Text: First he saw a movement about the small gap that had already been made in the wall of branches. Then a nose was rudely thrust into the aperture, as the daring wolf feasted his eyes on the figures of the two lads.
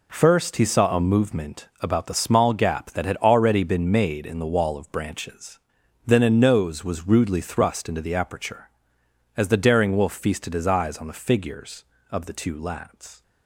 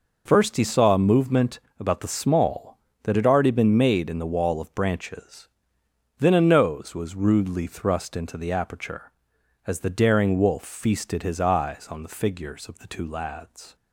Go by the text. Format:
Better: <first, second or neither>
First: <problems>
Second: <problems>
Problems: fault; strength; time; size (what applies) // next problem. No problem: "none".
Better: first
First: none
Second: pauses between "movement" and "about"; slight; at 1.6 s; 0.18 s long // skips "gap"; at 2.9 s